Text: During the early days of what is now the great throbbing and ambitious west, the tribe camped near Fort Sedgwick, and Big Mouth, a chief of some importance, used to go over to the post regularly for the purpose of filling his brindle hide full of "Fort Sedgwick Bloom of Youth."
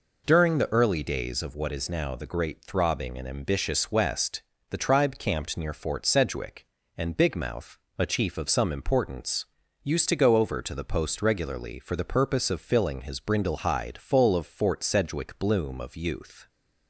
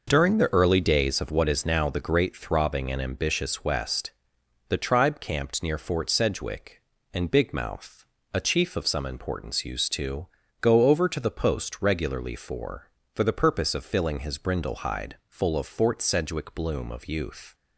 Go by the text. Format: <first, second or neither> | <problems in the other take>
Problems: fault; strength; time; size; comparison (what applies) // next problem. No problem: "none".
first | pauses between "to" and "go"; slight; at 10.2 s; 0.36 s long // says "for" twice; at 13.1 s